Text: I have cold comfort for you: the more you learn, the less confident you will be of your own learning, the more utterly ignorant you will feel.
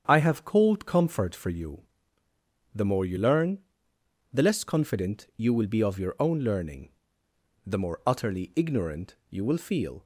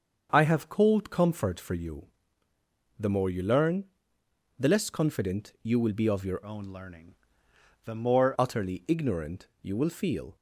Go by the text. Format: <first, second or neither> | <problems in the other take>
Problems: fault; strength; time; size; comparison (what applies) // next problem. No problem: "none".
first | starts louder than the rest; until 1.3 s; 6.5 dB; strong in the first // changes voice from "own" to "more"; from 6.4 to 8.3 s; 1.9 s long